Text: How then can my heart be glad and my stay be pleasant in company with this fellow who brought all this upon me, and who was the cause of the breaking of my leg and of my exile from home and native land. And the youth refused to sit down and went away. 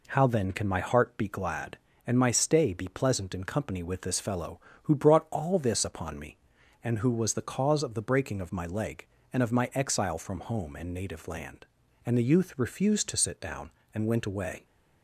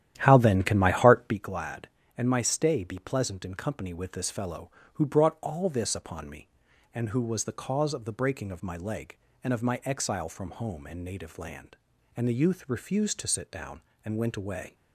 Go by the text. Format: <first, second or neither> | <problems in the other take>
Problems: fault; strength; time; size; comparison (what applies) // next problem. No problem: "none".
first | starts louder than the rest; strong; until 1.4 s; 11.5 dB